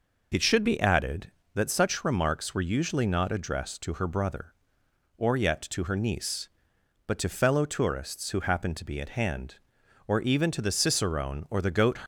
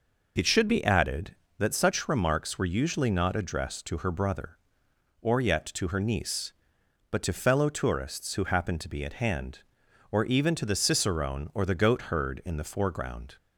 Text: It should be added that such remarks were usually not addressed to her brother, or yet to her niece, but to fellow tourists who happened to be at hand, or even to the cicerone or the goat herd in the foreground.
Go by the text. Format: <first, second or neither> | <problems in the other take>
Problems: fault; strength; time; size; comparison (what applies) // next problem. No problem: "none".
second | stops before "herd in the foreground"; at 12.0 s